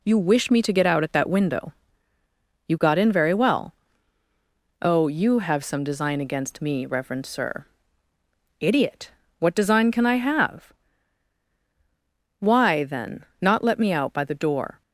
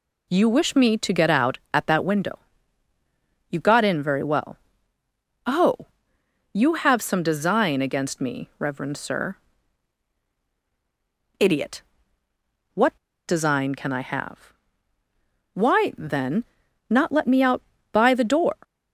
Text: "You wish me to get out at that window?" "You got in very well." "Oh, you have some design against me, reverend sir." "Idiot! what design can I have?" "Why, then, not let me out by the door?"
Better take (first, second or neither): first